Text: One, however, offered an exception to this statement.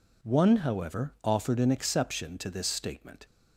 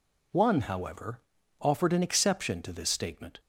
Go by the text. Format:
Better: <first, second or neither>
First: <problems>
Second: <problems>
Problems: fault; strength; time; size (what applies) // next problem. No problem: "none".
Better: neither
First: none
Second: none